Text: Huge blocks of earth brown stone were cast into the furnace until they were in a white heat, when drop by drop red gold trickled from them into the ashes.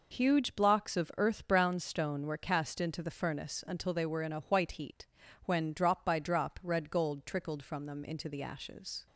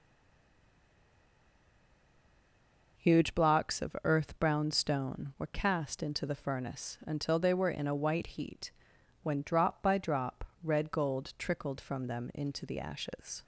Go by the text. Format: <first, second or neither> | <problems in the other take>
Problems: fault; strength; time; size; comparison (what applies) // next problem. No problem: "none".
first | stays silent before the first word; strong; until 2.9 s; 2.9 s long // pauses between "drop" and "red"; slight; at 10.4 s; 0.20 s long